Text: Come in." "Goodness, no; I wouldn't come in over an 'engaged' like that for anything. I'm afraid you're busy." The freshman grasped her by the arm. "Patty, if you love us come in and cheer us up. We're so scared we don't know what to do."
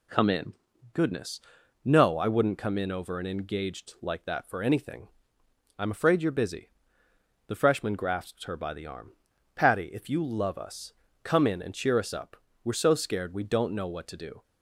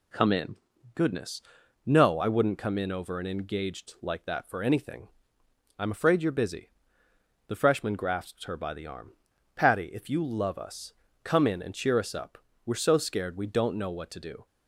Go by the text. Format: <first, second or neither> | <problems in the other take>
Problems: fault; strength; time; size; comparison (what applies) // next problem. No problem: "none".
neither | pauses between "us" and "come"; slight; the same in both